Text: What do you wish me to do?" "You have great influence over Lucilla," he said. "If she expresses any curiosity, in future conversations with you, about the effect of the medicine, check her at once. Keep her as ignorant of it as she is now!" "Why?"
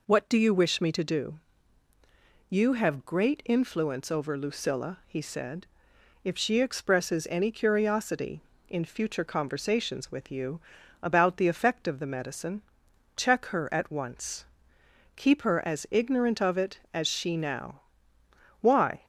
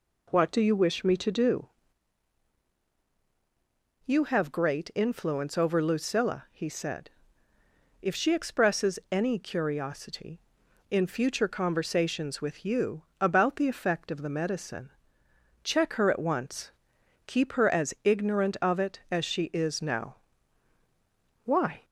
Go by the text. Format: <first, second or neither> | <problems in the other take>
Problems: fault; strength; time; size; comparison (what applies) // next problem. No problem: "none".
second | skips "is"; at 17.3 s